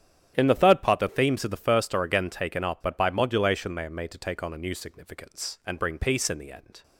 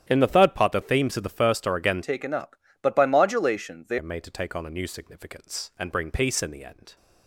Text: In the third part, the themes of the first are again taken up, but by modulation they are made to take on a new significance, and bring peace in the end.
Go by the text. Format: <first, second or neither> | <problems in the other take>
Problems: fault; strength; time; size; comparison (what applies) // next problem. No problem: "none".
first | starts louder than the rest; strong; until 1.1 s; 10 dB; strong in the first // changes voice from "taken" to "they"; from 2.0 to 3.9 s; 1.9 s long